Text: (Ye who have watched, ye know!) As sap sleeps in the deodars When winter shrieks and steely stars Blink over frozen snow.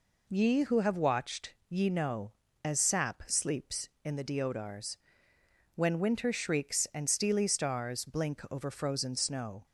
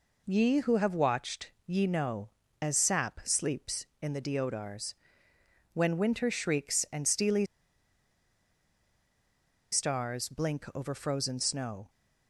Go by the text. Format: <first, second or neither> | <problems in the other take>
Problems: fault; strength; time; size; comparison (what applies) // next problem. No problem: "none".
first | pauses between "deodars" and "When"; noticeable; at 4.9 s; 0.80 s long; noticeable in the first // pauses between "steely" and "stars"; strong; at 7.4 s; 2.2 s long